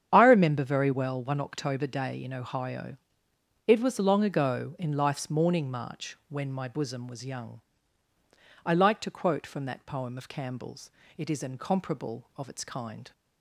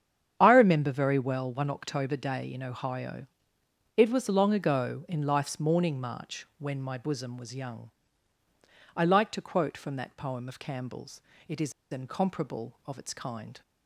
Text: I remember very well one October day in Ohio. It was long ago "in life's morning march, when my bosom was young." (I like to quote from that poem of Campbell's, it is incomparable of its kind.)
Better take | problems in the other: first | starts louder than the rest; strong; until 1.4 s; 8.5 dB; strong in the first // pauses between "is" and "incomparable"; slight; at 11.7 s; 0.18 s long

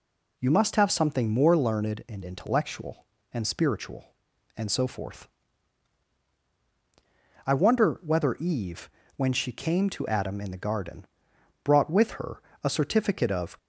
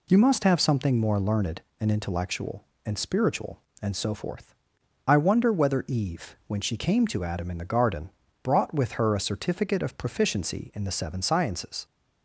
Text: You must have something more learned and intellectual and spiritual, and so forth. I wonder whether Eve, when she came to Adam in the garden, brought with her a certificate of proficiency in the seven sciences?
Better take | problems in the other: second | pauses between "her" and "a"; slight; at 12.4 s; 0.22 s long // stops before "proficiency in the seven sciences"; at 13.5 s

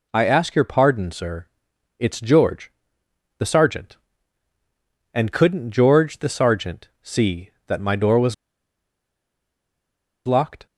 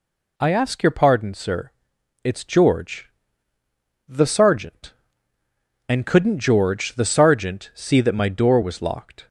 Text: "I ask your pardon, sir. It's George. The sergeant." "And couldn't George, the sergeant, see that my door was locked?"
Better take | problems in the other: second | pauses between "was" and "locked"; strong; at 8.3 s; 1.9 s long

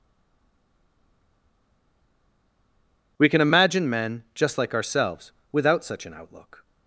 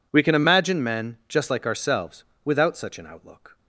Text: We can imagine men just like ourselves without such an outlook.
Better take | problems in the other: second | stays silent before the first word; strong; until 3.1 s; 3.1 s long // pauses between "ourselves" and "without"; slight; at 5.3 s; 0.21 s long; slight in the second

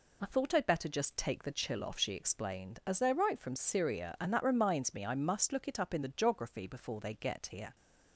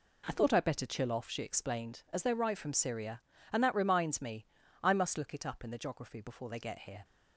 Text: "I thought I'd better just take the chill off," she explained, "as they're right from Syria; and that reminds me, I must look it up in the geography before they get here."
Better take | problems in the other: first | skips "just take the"; at 0.8 s

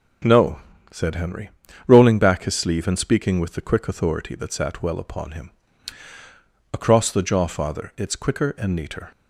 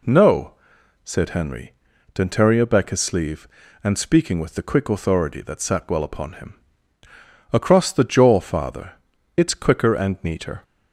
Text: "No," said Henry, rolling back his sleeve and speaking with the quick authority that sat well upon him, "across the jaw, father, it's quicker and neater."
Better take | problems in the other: first | says "dentaria" for "rolling"; at 2.1 s

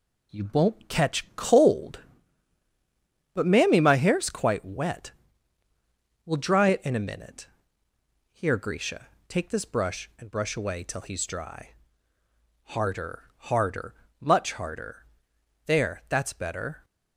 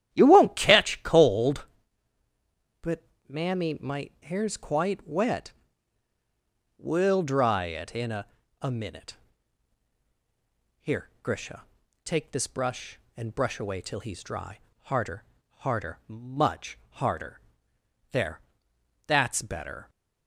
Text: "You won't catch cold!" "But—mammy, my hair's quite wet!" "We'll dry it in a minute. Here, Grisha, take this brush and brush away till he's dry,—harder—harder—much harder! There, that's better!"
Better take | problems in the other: first | starts louder than the rest; strong; until 1.1 s; 11 dB // says "a" twice; at 8.5 s

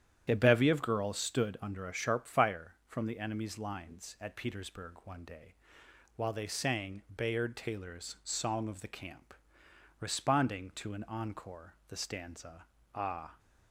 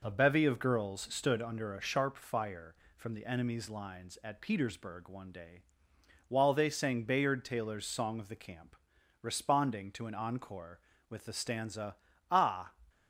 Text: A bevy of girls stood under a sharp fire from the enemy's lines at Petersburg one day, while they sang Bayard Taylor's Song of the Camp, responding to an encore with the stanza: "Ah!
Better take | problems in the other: second | starts louder than the rest; strong; until 1.3 s; 9.5 dB // pauses between "sang" and "Bayard"; slight; at 7.0 s; 0.16 s long // skips "with"; at 11.8 s

